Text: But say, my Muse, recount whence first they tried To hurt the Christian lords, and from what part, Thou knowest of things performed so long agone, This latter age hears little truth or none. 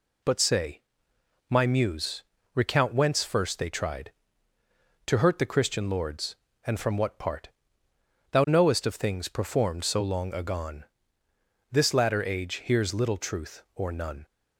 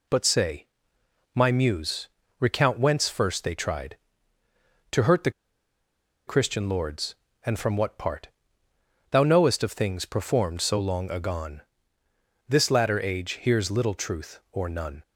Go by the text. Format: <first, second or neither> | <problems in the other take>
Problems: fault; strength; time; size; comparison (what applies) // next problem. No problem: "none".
first | pauses between "the" and "Christian"; noticeable; at 5.3 s; 0.95 s long